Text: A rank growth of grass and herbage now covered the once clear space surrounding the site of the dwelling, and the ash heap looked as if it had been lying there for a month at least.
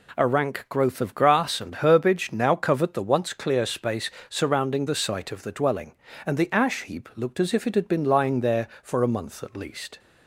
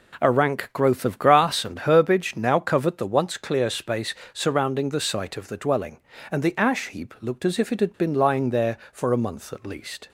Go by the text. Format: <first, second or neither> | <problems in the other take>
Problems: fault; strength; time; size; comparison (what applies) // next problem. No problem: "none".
first | starts louder than the rest; slight; until 2.0 s; 3.5 dB // pauses between "space" and "surrounding"; slight; at 4.1 s; 0.18 s long; slight in the first